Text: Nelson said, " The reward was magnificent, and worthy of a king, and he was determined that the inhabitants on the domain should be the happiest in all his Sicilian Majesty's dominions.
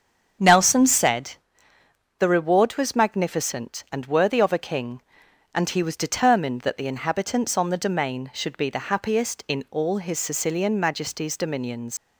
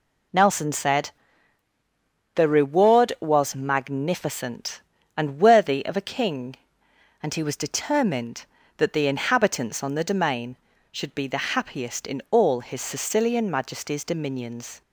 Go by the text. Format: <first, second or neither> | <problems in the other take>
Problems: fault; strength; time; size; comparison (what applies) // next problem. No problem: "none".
second | starts louder than the rest; until 1.8 s; 7 dB // leaves "dominions" unfinished; at 11.9 s; 110 ms